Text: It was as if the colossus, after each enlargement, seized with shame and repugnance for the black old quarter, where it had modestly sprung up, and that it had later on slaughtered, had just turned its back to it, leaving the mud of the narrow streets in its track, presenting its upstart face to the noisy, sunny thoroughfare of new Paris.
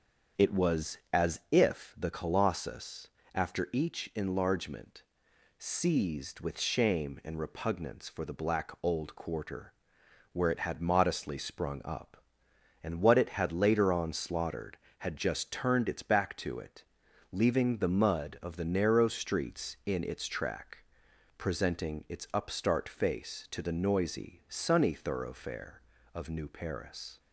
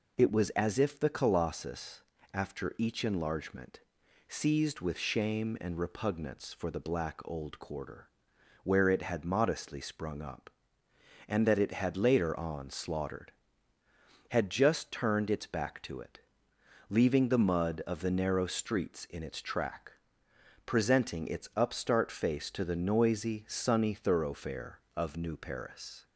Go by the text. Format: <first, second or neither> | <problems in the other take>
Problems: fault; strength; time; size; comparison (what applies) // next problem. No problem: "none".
second | starts louder than the rest; until 1.6 s; 7 dB // says "what" for "that"; at 13.0 s